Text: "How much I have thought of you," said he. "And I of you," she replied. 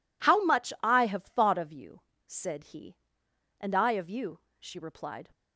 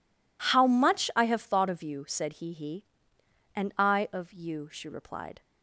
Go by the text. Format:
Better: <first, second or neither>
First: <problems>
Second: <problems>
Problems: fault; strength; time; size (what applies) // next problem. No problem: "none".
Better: first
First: none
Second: says "he" twice; at 2.5 s